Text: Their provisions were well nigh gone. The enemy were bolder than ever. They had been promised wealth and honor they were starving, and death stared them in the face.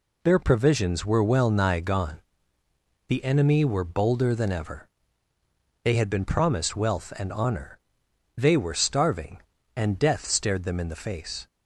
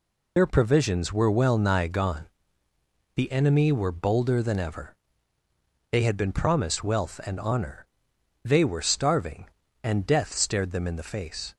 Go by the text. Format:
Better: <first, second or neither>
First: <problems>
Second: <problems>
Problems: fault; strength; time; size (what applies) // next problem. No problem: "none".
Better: first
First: pauses between "honor" and "they"; noticeable; at 7.7 s; 0.58 s long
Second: loses the start of "Their"; at 0.3 s; 65 ms // pauses between "honor" and "they"; noticeable; at 7.8 s; 0.58 s long